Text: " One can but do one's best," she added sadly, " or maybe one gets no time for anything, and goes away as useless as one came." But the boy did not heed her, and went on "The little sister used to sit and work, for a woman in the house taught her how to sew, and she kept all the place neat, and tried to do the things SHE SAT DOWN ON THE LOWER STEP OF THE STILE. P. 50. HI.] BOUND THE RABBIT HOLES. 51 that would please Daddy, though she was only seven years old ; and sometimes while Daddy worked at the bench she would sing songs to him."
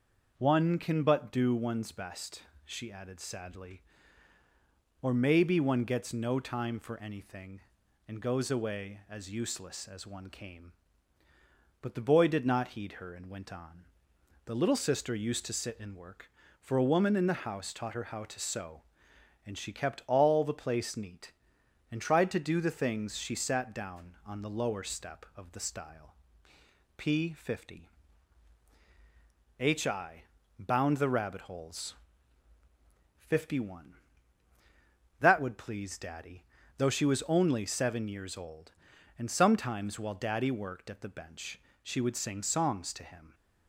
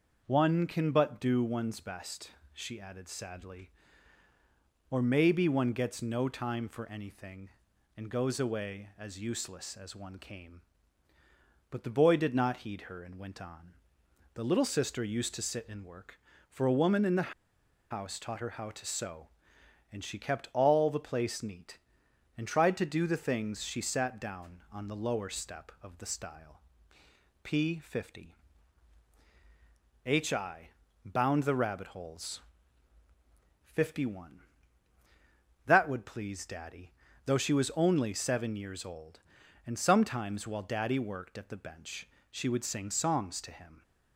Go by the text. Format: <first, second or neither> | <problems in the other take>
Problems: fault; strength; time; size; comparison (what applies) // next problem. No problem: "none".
first | starts louder than the rest; until 1.2 s; 6.5 dB; also in the first // pauses between "on" and "The"; noticeable; at 13.7 s; 0.58 s long; noticeable in the first // pauses between "the" and "house"; noticeable; at 17.3 s; 0.57 s long // pauses between "bench" and "she"; slight; at 42.0 s; 0.24 s long; slight in the first